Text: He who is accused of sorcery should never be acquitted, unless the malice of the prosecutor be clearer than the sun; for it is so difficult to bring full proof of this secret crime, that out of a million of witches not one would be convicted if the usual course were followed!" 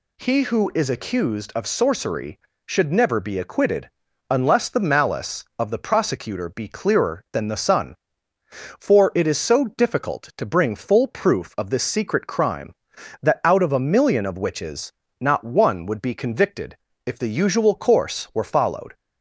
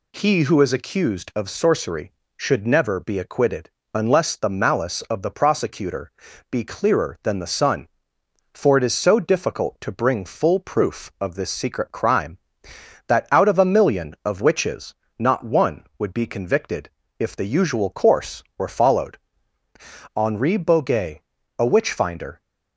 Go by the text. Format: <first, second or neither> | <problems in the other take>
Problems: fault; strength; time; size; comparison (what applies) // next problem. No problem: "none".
first | pauses between "prosecutor" and "be"; at 6.1 s; 0.40 s long // pauses between "witches" and "not"; slight; at 14.9 s; 0.22 s long; slight in the first // pauses between "convicted" and "if"; slight; at 16.9 s; 0.26 s long; slight in the first // goes on to say "Henri Boguet a witch finder"; strong; from 20.1 s on; 2.2 s long